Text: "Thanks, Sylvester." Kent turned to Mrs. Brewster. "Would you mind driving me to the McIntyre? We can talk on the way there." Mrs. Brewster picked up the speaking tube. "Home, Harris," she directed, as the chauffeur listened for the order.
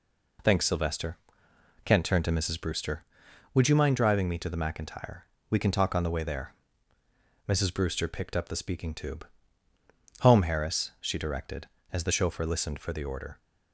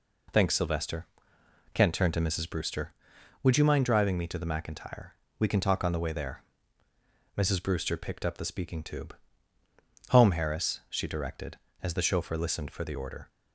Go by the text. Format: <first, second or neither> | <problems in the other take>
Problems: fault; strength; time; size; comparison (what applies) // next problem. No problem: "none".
neither | none